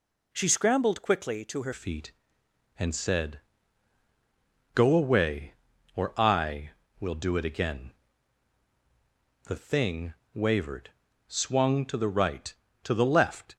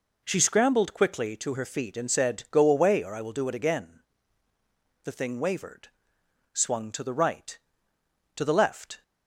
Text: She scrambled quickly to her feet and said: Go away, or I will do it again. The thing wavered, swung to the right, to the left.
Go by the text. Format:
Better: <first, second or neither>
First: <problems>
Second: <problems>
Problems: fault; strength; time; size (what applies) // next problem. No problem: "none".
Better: second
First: changes voice at "feet"; from 1.7 s on; 11.8 s long // pauses between "thing" and "wavered"; slight; at 10.1 s; 0.20 s long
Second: none